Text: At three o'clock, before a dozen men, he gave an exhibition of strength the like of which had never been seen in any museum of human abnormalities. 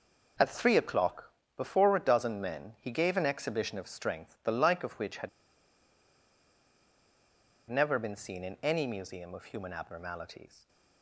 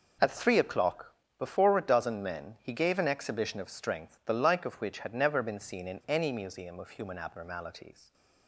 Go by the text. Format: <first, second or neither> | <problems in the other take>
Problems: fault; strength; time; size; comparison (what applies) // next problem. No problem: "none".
second | pauses between "had" and "never"; strong; at 5.2 s; 2.4 s long